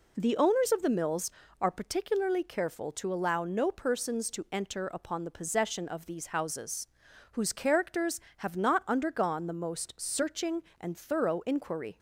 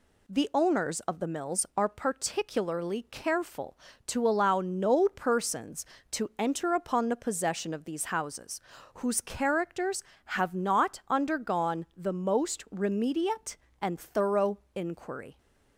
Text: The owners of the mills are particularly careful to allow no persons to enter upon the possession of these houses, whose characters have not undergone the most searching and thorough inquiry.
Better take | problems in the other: first | says "remediate" for "searching"; at 12.6 s // pauses between "thorough" and "inquiry"; slight; at 14.5 s; 0.16 s long

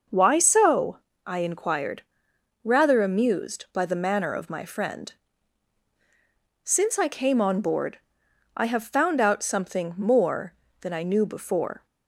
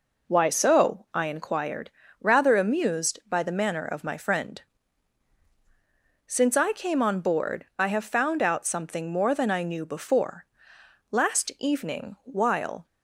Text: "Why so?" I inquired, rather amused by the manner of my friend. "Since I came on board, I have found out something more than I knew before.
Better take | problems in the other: first | goes on to say "Last evening while"; strong; from 11.1 s on; 1.7 s long

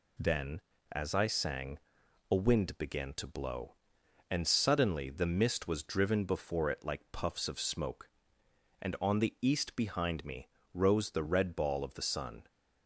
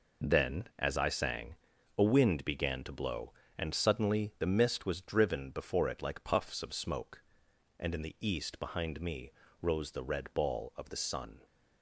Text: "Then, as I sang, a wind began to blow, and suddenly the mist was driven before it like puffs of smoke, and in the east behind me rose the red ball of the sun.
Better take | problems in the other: second | says "on" for "in"; at 8.9 s // pauses between "me" and "rose"; slight; at 10.4 s; 0.26 s long; slight in the second

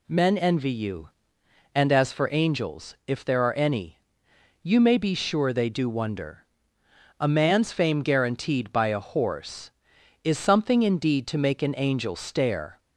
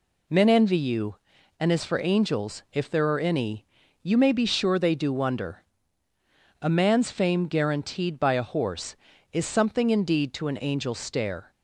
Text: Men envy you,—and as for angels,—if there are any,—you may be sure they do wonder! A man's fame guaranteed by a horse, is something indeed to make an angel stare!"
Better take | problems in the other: first | skips "make"; at 10.4 s

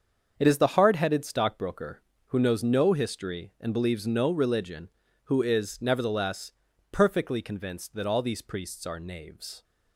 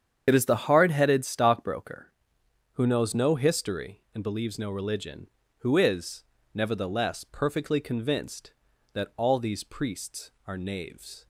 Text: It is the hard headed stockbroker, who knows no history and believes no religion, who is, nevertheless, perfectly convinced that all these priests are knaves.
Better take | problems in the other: first | loses the start of "It"; at 0.2 s; 45 ms // starts louder than the rest; strong; until 1.3 s; 8 dB; also in the first

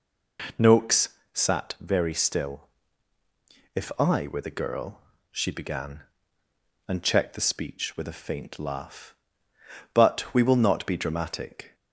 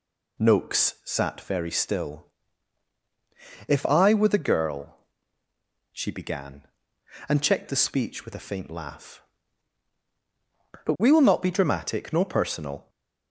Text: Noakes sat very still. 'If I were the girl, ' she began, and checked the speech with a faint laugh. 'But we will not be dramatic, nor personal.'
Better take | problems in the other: second | pauses between "Noakes" and "sat"; slight; at 1.0 s; 0.26 s long // stops before "nor personal"; at 11.7 s

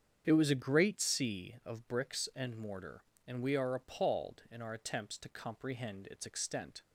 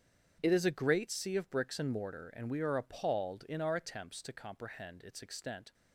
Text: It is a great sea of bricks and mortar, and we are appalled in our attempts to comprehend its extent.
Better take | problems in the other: second | starts louder than the rest; strong; until 1.2 s; 8 dB; strong in the second // says "was" for "is"; at 0.3 s

